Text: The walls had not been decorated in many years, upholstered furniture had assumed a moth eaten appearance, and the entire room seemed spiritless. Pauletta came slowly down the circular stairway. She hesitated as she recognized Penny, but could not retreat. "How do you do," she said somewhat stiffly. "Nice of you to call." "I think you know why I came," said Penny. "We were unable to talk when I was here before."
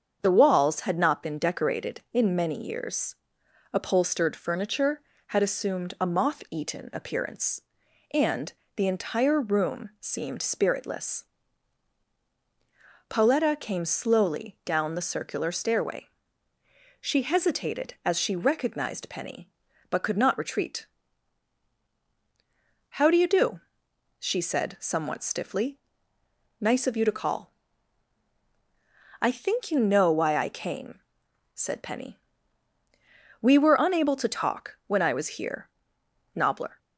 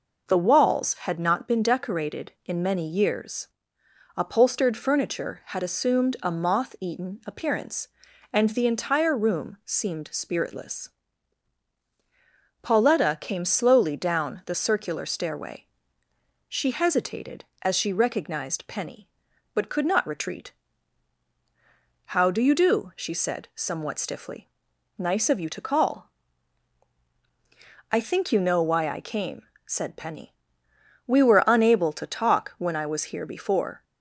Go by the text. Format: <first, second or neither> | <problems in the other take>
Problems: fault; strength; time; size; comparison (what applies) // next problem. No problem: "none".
second | starts louder than the rest; until 1.2 s; 7 dB // pauses between "and" and "the"; slight; at 8.5 s; 0.22 s long // says "nobbler" for "before"; at 36.3 s